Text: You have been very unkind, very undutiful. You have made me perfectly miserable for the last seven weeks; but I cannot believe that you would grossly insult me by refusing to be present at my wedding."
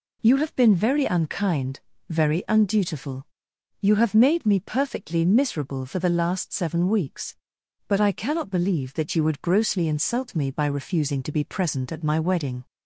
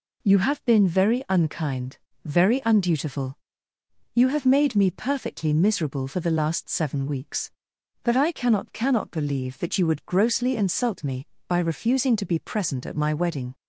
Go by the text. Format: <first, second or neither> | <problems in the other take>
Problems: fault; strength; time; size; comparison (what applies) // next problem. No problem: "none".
first | says "cannot" twice; at 8.7 s